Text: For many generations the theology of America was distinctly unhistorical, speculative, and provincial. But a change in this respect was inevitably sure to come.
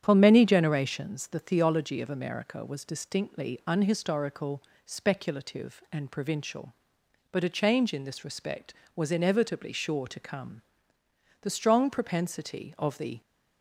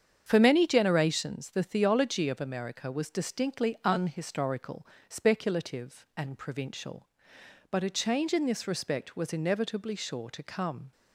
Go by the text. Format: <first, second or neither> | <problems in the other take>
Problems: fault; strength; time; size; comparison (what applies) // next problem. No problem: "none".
second | starts louder than the rest; strong; until 1.0 s; 9 dB; strong in the second // goes on to say "The strong propensity of the"; strong; from 11.4 s on; 1.8 s long